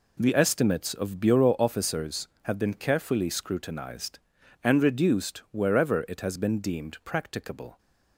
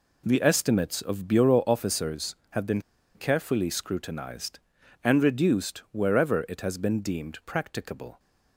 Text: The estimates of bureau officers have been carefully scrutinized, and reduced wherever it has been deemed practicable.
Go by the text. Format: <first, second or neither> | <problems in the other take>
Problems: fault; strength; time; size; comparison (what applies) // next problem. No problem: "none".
first | pauses between "been" and "carefully"; slight; at 2.8 s; 0.34 s long